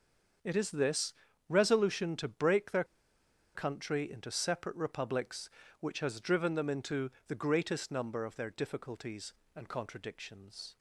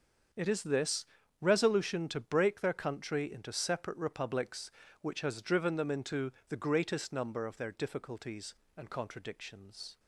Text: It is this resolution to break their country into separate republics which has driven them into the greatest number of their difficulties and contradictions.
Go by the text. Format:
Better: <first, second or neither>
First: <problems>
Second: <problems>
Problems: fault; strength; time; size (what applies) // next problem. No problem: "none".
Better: second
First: starts louder than the rest; until 1.7 s; 6.5 dB // pauses between "this" and "resolution"; slight; at 1.1 s; 0.36 s long // pauses between "their" and "country"; noticeable; at 2.8 s; 0.71 s long // pauses between "into" and "the"; slight; at 7.0 s; 0.18 s long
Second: starts louder than the rest; until 1.7 s; 7 dB // pauses between "this" and "resolution"; slight; at 1.0 s; 0.36 s long // pauses between "into" and "the"; slight; at 6.3 s; 0.18 s long